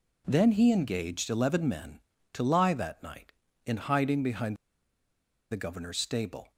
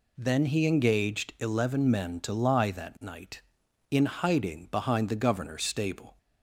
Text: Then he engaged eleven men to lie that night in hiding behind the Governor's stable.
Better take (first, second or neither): second